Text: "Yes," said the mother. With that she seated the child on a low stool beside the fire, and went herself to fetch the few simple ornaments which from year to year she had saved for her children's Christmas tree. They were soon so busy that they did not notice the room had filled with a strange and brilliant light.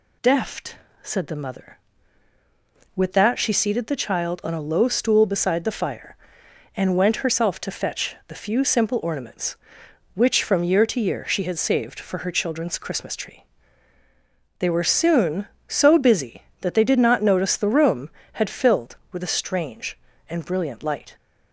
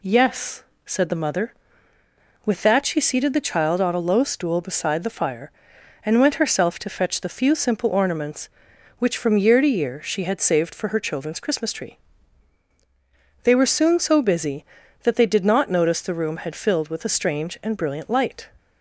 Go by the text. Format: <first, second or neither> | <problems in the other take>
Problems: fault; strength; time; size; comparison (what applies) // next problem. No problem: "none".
second | says "Deft" for "Yes"; at 0.2 s